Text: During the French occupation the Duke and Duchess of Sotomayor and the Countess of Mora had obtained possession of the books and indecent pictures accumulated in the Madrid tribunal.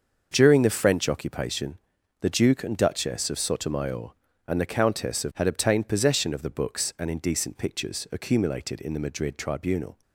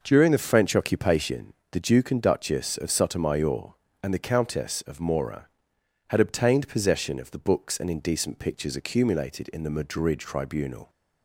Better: second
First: starts louder than the rest; until 1.3 s; 6.5 dB // pauses between "occupation" and "the"; at 1.7 s; 0.44 s long // skips "Mora"; at 5.3 s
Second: pauses between "occupation" and "the"; slight; at 1.5 s; 0.20 s long

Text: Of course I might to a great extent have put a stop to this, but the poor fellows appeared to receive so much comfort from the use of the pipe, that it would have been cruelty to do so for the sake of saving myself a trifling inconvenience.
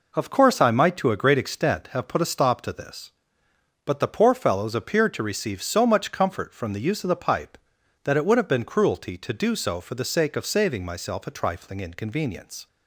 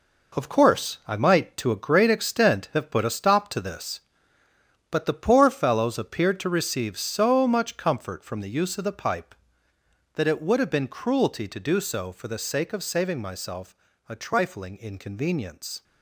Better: first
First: none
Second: gets quieter; strong; throughout; 8.5 dB // pauses between "myself" and "a"; slight; at 13.7 s; 0.34 s long

